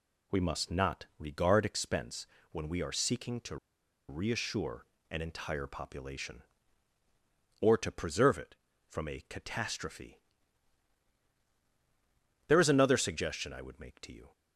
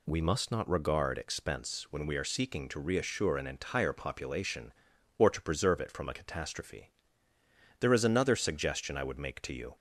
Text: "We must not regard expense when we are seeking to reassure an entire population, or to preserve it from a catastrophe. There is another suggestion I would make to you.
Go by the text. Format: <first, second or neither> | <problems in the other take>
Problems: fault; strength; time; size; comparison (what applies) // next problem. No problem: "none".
second | pauses between "expense" and "when"; slight; at 2.2 s; 0.24 s long // pauses between "to" and "reassure"; noticeable; at 3.5 s; 0.52 s long // pauses between "reassure" and "an"; slight; at 4.8 s; 0.24 s long